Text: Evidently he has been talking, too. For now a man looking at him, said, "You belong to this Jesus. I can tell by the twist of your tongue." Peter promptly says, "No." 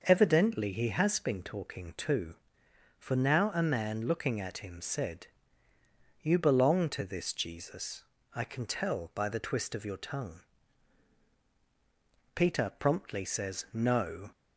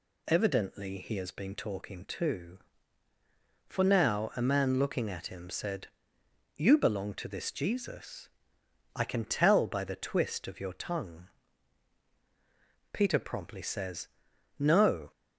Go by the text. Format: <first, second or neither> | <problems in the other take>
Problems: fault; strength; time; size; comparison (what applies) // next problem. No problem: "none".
neither | none